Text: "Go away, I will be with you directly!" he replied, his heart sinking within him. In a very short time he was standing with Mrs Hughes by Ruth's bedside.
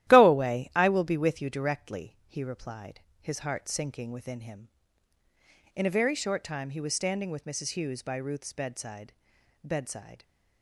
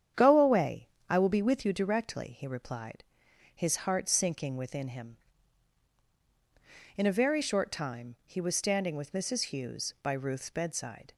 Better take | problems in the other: second | starts louder than the rest; strong; until 1.1 s; 13.5 dB; strong in the second // says "bedside" twice; at 9.6 s

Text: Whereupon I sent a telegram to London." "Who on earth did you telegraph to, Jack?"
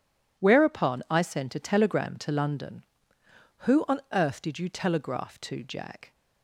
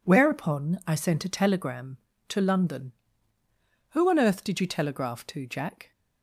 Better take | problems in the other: neither | none

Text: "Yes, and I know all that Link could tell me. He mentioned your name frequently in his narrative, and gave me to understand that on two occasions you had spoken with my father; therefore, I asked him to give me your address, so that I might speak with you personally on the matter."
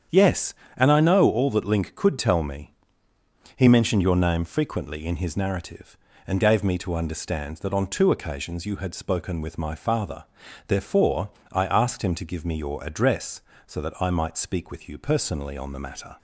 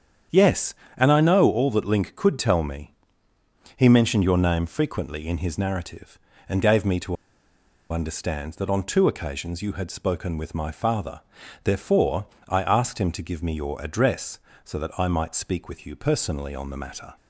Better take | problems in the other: first | starts louder than the rest; strong; until 1.5 s; 8 dB; strong in the first // pauses between "to" and "understand"; noticeable; at 7.1 s; 0.76 s long

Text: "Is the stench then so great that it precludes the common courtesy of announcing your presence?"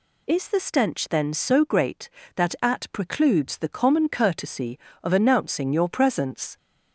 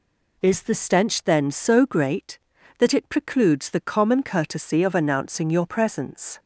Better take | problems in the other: second | says "at" for "it"; at 2.6 s

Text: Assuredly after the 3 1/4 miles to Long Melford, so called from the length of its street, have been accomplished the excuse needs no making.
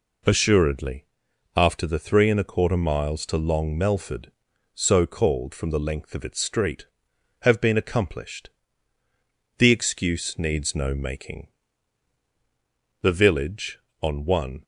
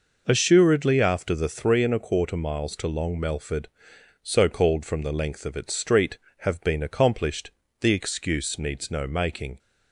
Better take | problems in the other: second | pauses between "Assuredly" and "after"; noticeable; at 1.0 s; 0.50 s long // pauses between "accomplished" and "the"; at 8.4 s; 1.1 s long; slight in the second // goes on to say "The village on one"; from 13.0 s on; 1.6 s long

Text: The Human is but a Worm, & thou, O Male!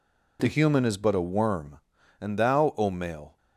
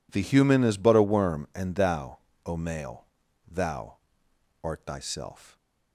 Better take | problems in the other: first | goes on to say "Thou art Thyself"; strong; from 3.4 s on; 2.0 s long

